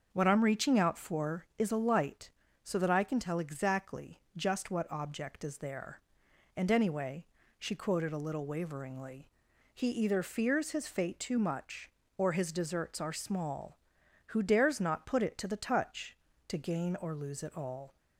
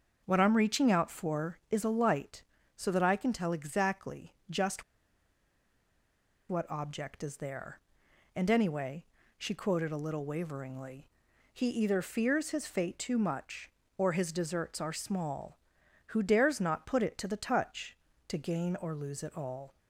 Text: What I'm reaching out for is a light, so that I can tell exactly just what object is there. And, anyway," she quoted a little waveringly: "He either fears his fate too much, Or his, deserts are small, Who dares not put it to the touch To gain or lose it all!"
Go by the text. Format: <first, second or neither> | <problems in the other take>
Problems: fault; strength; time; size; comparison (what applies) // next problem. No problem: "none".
first | starts louder than the rest; until 1.2 s; 6.5 dB; also in the first // pauses between "exactly" and "just"; slight; at 4.3 s; 0.16 s long; slight in the first // pauses between "just" and "what"; strong; at 4.8 s; 1.6 s long